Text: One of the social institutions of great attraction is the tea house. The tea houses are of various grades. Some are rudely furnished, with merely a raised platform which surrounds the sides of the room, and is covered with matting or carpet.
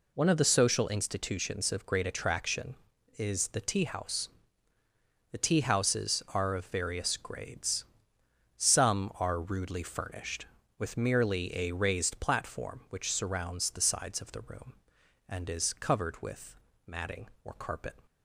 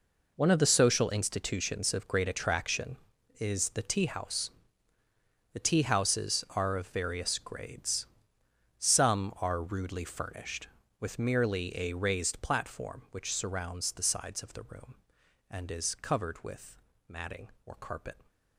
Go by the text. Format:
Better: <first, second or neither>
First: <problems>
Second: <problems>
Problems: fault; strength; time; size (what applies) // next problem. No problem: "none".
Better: first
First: pauses between "with" and "matting"; slight; at 16.5 s; 0.30 s long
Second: gets quieter; strong; throughout; 13 dB // pauses between "with" and "matting"; slight; at 16.7 s; 0.30 s long